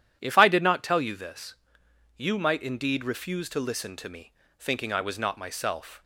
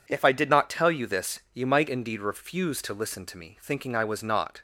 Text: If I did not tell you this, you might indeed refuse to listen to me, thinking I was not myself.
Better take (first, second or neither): first